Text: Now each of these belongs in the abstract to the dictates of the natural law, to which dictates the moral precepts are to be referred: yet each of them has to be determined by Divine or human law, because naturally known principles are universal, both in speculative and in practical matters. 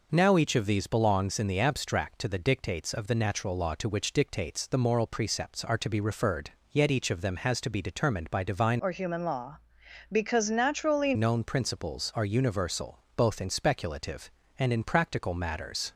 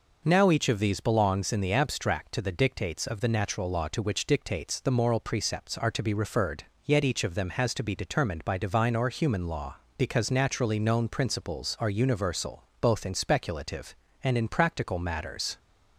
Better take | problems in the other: second | changes voice from "or" to "naturally"; from 8.7 to 11.1 s; 2.4 s long

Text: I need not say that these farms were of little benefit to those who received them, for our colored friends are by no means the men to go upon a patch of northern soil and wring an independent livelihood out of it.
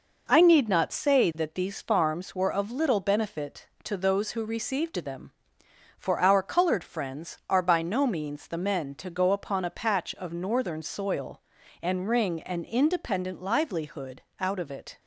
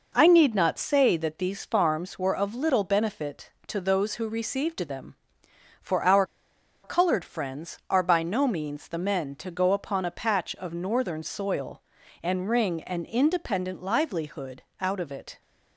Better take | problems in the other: first | pauses between "our" and "colored"; noticeable; at 6.2 s; 0.60 s long // pauses between "livelihood" and "out"; slight; at 14.6 s; 0.16 s long; slight in the first

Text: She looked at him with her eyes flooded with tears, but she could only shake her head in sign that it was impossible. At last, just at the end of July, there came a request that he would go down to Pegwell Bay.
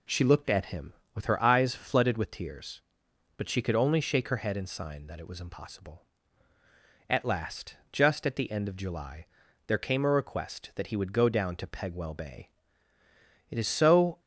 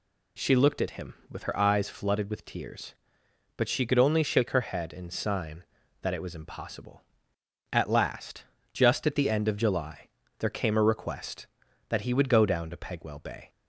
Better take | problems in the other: second | goes on to say "It is so"; noticeable; from 13.4 s on; 0.70 s long

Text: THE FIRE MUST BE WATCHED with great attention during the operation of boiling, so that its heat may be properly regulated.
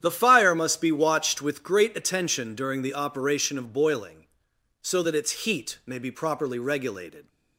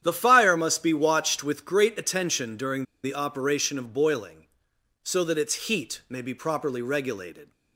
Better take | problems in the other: first | starts louder than the rest; strong; until 1.0 s; 9.5 dB; strong in the first // pauses between "during" and "the"; slight; at 2.8 s; 0.21 s long

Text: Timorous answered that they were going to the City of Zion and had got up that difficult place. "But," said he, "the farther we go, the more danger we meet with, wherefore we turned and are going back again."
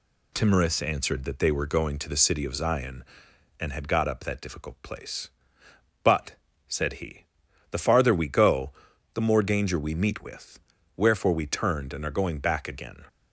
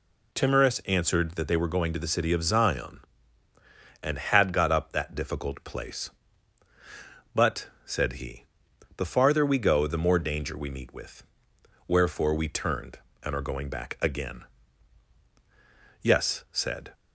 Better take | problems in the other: first | goes on to say "Yes said"; noticeable; from 16.0 s on; 0.92 s long

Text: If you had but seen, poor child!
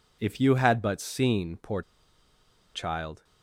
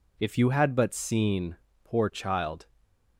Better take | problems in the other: second | pauses between "poor" and "child"; noticeable; at 1.8 s; 0.92 s long

